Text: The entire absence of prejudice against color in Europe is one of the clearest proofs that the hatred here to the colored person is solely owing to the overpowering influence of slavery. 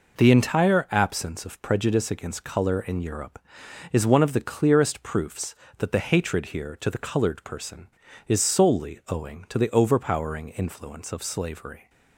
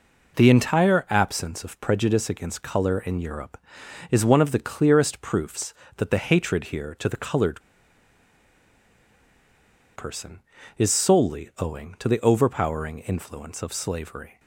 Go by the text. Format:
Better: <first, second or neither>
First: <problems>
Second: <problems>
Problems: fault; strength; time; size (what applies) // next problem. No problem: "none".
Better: first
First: none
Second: pauses between "colored" and "person"; strong; at 7.6 s; 2.3 s long